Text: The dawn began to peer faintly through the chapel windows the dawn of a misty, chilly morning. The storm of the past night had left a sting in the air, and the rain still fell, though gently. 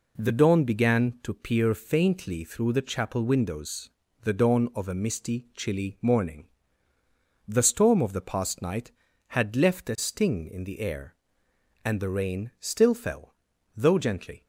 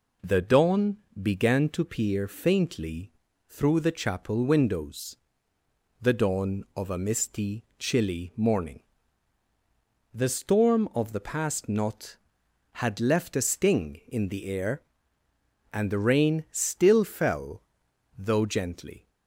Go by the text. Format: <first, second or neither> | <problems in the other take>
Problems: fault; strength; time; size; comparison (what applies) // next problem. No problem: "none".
first | pauses between "dawn" and "began"; slight; at 0.9 s; 0.22 s long // pauses between "faintly" and "through"; slight; at 3.1 s; 0.36 s long // pauses between "windows" and "the"; noticeable; at 5.1 s; 0.86 s long; slight in the first // says "knot" for "night"; at 11.6 s